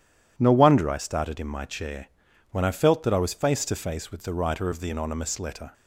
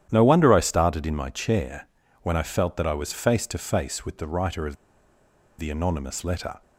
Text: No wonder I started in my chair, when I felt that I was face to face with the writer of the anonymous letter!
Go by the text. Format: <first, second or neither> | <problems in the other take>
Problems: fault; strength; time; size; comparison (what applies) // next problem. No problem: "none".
first | starts louder than the rest; strong; until 1.1 s; 11 dB // pauses between "of" and "the"; noticeable; at 4.7 s; 0.83 s long